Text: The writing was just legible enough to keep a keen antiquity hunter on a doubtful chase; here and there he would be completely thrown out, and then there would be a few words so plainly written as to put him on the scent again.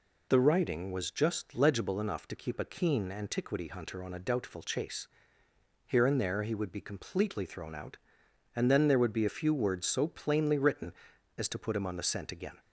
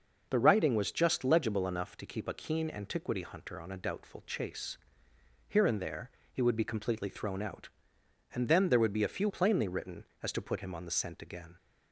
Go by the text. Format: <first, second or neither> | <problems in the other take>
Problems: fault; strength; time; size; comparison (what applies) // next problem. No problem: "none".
first | pauses between "there" and "he"; slight; at 6.1 s; 0.22 s long // skips "words so"; at 9.2 s